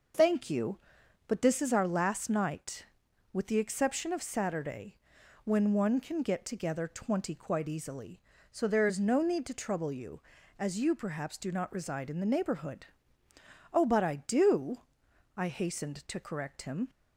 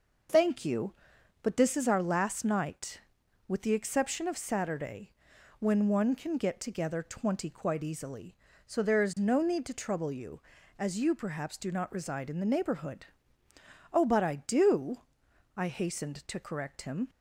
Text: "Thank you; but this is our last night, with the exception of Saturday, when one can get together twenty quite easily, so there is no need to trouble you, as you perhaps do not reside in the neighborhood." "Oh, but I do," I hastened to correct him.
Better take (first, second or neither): neither